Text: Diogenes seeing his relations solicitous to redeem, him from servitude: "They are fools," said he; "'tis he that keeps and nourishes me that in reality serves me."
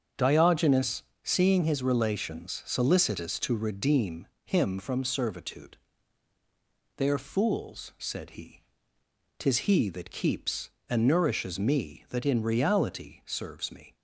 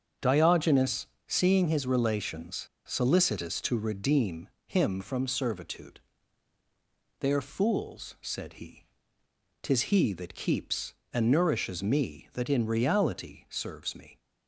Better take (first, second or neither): first